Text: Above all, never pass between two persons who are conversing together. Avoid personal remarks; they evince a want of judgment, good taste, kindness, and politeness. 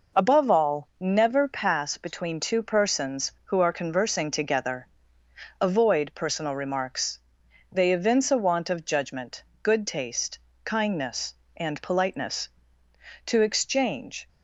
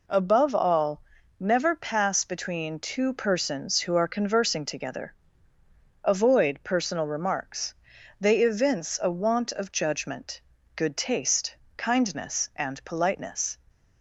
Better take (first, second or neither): second